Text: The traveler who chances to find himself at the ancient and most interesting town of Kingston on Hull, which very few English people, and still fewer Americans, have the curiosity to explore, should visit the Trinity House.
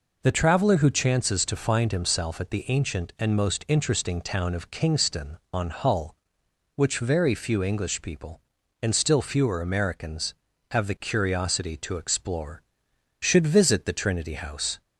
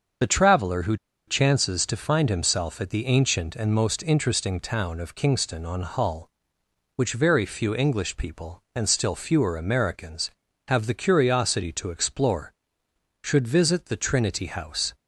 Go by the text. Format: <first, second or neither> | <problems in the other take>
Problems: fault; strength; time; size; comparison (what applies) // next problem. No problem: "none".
first | starts louder than the rest; until 1.5 s; 7 dB // pauses between "who" and "chances"; slight; at 0.9 s; 0.32 s long